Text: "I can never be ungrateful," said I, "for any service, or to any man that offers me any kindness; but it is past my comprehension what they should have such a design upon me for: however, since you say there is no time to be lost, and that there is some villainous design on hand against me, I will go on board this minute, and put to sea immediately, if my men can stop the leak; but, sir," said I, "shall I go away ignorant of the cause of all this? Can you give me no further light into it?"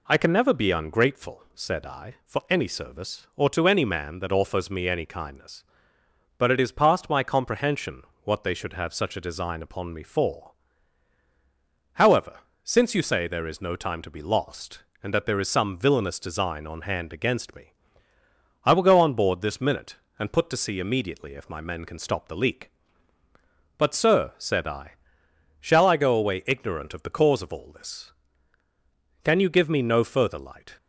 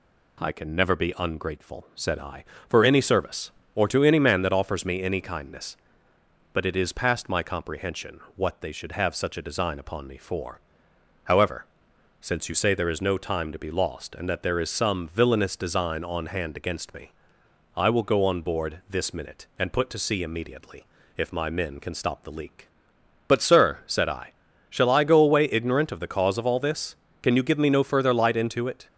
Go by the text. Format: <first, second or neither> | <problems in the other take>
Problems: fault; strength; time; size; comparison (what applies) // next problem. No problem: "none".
second | pauses between "comprehension" and "what"; slight; at 8.0 s; 0.20 s long; slight in the second // stops before "into it"; at 30.7 s